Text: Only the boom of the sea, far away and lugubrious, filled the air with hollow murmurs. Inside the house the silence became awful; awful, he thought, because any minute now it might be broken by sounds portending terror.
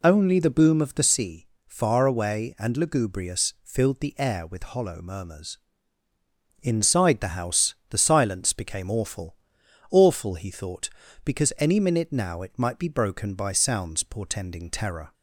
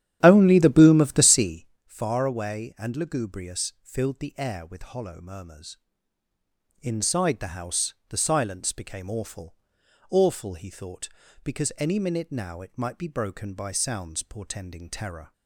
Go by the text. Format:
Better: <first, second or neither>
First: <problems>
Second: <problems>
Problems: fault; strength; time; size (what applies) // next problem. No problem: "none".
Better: first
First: pauses between "house" and "the"; slight; at 7.7 s; 0.16 s long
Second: starts louder than the rest; strong; until 1.9 s; 11 dB // pauses between "house" and "the"; slight; at 7.9 s; 0.16 s long